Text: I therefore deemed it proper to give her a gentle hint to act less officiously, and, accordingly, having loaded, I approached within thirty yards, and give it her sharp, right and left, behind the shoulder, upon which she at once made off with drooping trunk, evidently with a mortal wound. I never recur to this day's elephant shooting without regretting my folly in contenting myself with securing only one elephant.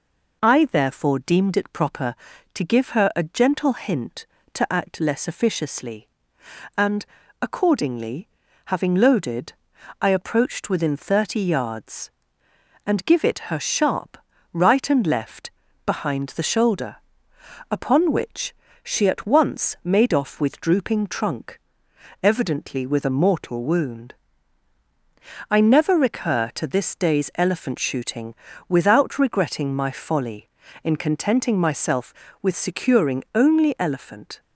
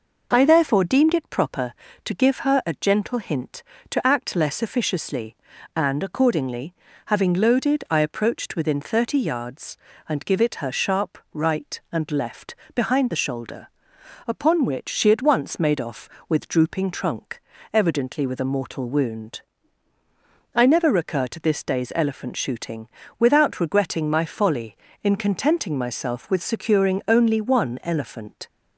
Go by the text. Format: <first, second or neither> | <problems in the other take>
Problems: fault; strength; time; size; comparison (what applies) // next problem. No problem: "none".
second | pauses between "which" and "she"; slight; at 18.5 s; 0.30 s long // pauses between "shooting" and "without"; slight; at 28.3 s; 0.36 s long; slight in the second // skips "one"; at 33.7 s